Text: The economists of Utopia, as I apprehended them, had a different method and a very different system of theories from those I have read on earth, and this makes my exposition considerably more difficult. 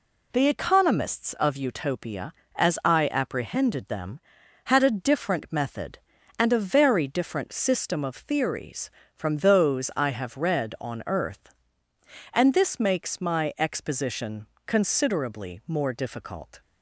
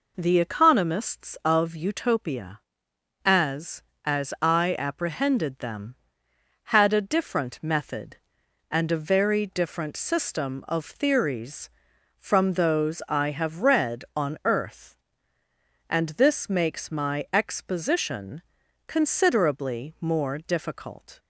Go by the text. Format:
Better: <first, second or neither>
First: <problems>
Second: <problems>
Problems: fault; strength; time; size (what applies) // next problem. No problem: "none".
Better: first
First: pauses between "exposition" and "considerably"; slight; at 14.4 s; 0.20 s long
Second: says "as" twice; at 4.0 s // pauses between "exposition" and "considerably"; noticeable; at 18.4 s; 0.46 s long